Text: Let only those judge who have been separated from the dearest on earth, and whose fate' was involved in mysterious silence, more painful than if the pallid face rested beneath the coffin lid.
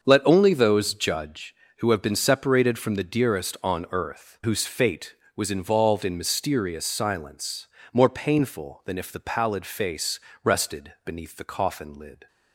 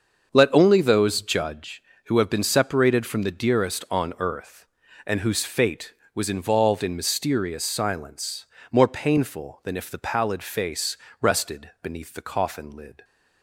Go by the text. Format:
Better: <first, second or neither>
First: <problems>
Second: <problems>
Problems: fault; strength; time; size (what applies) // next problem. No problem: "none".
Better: second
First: starts louder than the rest; until 1.0 s; 6.5 dB // skips "and"; at 4.4 s // pauses between "face" and "rested"; slight; at 10.2 s; 0.24 s long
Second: starts louder than the rest; until 1.3 s; 6.5 dB // pauses between "face" and "rested"; slight; at 10.9 s; 0.24 s long